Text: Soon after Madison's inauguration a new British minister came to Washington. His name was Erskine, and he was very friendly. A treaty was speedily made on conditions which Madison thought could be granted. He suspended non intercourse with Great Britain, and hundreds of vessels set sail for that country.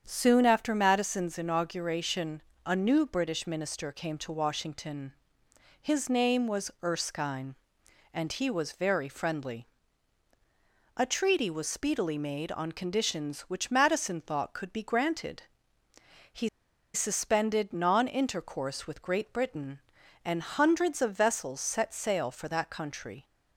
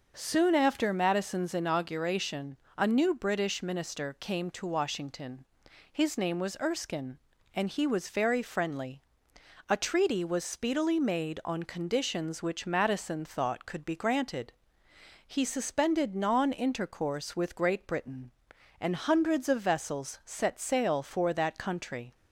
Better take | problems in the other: second | starts louder than the rest; strong; until 1.0 s; 8 dB // pauses between "inauguration" and "a"; slight; at 2.4 s; 0.20 s long; slight in the second // pauses between "He" and "suspended"; at 16.4 s; 0.45 s long

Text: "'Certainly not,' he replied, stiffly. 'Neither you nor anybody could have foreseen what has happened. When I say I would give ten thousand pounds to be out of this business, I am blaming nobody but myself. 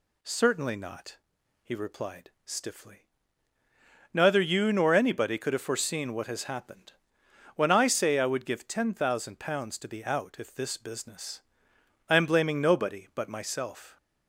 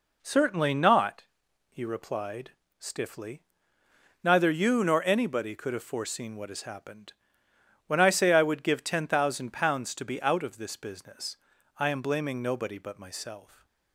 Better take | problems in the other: second | says "if" for "of"; at 10.3 s

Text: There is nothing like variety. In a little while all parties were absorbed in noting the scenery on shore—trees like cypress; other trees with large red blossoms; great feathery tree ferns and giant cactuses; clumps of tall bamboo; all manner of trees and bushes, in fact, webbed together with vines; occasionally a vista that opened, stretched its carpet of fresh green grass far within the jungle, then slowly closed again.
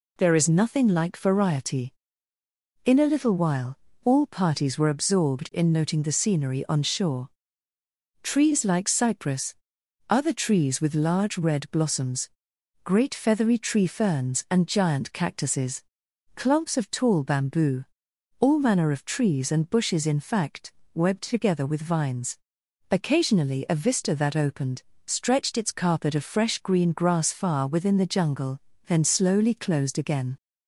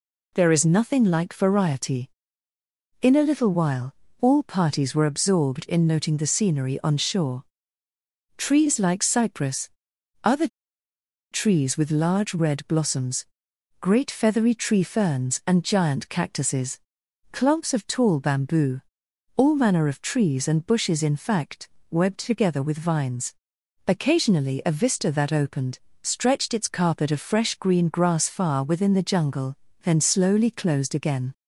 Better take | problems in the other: first | pauses between "while" and "all"; slight; at 3.9 s; 0.28 s long; slight in the first // pauses between "other" and "trees"; noticeable; at 10.4 s; 0.84 s long

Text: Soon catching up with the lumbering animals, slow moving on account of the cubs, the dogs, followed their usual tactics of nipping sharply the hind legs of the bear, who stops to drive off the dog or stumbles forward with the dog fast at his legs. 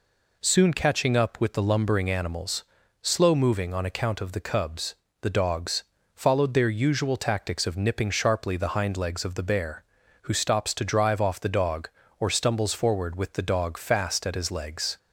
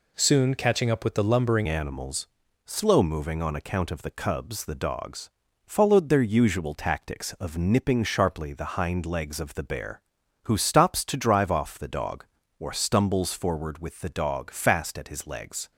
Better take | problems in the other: first | changes voice at "animals"; from 1.6 s on; 14.1 s long

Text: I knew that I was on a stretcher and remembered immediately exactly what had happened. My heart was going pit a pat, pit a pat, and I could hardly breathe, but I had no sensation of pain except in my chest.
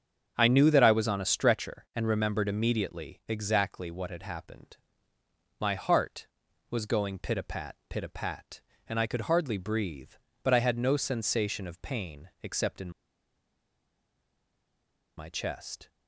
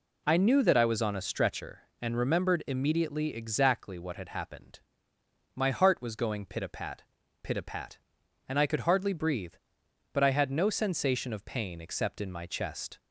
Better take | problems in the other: second | starts louder than the rest; until 1.3 s; 7 dB // pauses between "in" and "my"; strong; at 12.8 s; 2.2 s long

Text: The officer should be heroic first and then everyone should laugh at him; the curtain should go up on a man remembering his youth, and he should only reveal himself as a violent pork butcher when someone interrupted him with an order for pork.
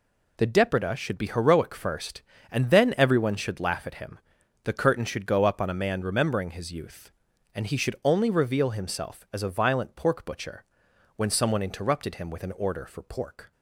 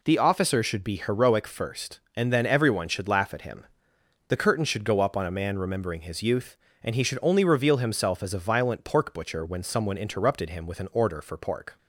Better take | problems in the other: second | says "depreda" for "officer"; at 0.4 s // pauses between "butcher" and "when"; noticeable; at 10.6 s; 0.54 s long

